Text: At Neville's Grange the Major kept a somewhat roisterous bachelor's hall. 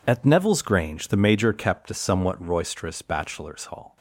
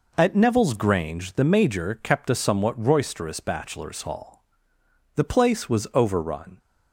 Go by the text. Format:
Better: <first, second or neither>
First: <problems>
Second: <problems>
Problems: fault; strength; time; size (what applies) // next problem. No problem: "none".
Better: first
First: none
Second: goes on to say "The place was overrun"; from 5.1 s on; 1.4 s long